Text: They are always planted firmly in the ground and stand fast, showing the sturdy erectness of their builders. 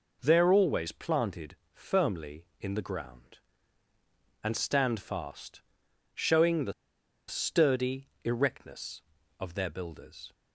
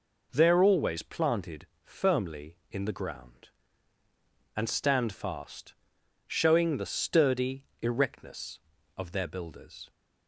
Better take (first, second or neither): second